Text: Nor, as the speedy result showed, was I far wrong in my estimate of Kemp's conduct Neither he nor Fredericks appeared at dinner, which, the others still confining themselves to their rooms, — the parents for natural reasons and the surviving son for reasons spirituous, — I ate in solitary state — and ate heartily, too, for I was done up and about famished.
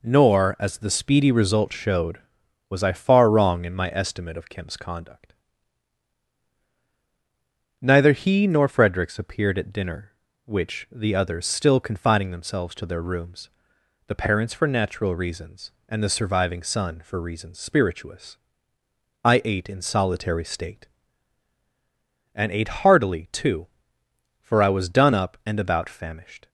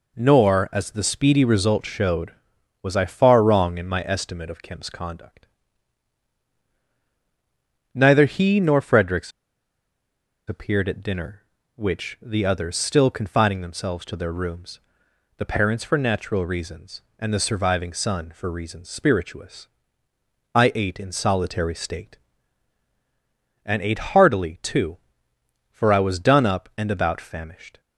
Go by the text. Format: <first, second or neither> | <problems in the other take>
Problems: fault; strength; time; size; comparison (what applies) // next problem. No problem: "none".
first | pauses between "conduct" and "Neither"; strong; at 5.4 s; 2.4 s long; strong in the first // pauses between "Fredericks" and "appeared"; at 9.3 s; 1.1 s long